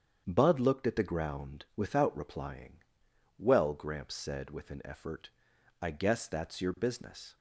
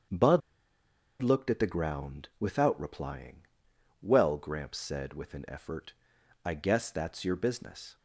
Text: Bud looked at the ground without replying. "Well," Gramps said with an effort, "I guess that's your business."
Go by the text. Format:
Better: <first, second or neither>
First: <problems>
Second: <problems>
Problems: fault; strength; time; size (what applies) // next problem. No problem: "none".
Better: first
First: starts louder than the rest; strong; until 1.2 s; 8 dB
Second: starts louder than the rest; strong; until 1.9 s; 8 dB // pauses between "Bud" and "looked"; noticeable; at 0.4 s; 0.80 s long